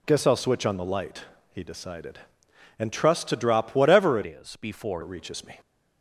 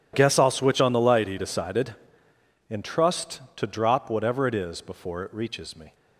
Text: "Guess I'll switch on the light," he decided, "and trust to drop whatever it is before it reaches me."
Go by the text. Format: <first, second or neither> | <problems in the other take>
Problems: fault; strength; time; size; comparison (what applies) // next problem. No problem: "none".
second | changes voice from "is" to "before"; from 4.2 to 5.0 s; 0.8 s long